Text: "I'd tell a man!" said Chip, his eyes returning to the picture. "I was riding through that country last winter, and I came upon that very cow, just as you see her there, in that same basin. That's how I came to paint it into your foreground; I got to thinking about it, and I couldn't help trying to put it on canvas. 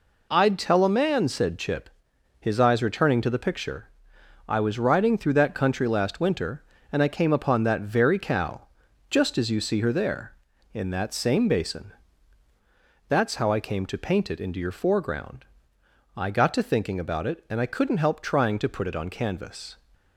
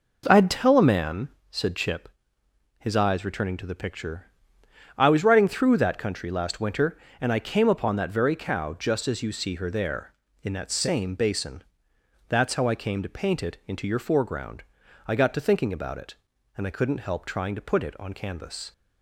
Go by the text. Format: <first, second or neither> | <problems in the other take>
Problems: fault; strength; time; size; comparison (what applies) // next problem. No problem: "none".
neither | none